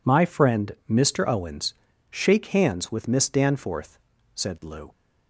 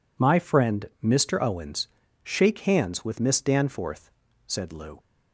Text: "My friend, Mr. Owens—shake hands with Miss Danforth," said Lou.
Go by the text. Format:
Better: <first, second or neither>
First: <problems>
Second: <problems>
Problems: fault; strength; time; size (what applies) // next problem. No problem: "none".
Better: neither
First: none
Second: none